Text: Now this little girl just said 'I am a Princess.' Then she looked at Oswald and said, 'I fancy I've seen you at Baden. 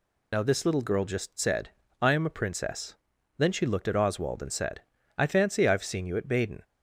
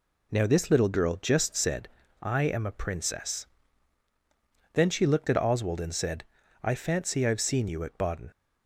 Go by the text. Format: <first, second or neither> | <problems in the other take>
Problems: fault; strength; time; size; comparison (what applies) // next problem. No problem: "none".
second | loses the start of "Now"; at 0.3 s; 20 ms // pauses between "said" and "I"; slight; at 1.7 s; 0.30 s long; slight in the second